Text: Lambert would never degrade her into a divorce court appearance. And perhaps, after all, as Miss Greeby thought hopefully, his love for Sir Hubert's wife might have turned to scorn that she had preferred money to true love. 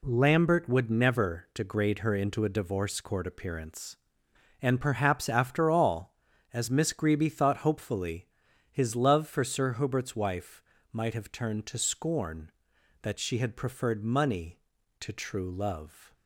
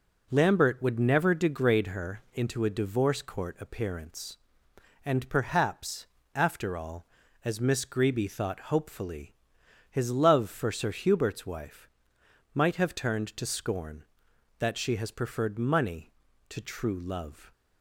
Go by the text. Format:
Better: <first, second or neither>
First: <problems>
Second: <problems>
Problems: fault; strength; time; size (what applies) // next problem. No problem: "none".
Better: first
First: pauses between "wife" and "might"; slight; at 10.6 s; 0.30 s long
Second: pauses between "wife" and "might"; noticeable; at 11.8 s; 0.66 s long // says "has" for "had"; at 14.9 s